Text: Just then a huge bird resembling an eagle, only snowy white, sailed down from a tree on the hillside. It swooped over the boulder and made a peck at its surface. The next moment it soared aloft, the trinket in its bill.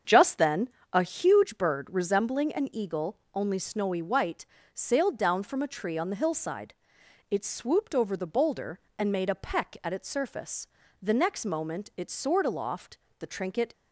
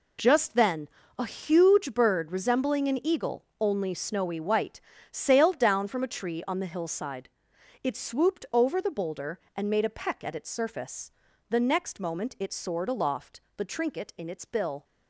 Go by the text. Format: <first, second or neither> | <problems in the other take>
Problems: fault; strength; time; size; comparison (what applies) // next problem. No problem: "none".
second | starts louder than the rest; strong; until 1.3 s; 7.5 dB // pauses between "then" and "a"; slight; at 0.6 s; 0.24 s long; slight in the second // stops before "in its bill"; at 13.7 s